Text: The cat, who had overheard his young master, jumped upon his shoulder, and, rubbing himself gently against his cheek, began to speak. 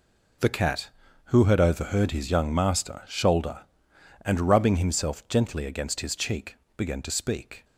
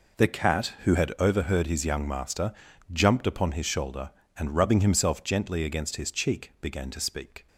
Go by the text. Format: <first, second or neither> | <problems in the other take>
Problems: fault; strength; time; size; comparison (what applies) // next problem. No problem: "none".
second | skips "jumped upon his"; at 3.0 s